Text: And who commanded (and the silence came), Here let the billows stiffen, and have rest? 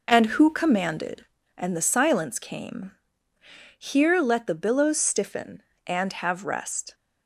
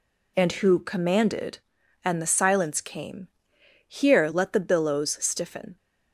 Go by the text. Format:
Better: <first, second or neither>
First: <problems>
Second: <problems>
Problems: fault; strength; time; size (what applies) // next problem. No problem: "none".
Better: first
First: none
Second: stops before "and have rest"; at 5.7 s